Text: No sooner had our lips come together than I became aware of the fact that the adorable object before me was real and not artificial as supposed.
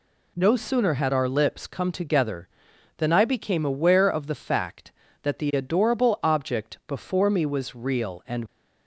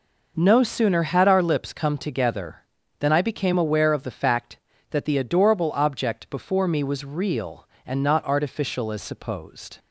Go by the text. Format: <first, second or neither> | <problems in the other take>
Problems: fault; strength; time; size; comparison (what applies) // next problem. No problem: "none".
second | stops before "not artificial as supposed"; at 8.4 s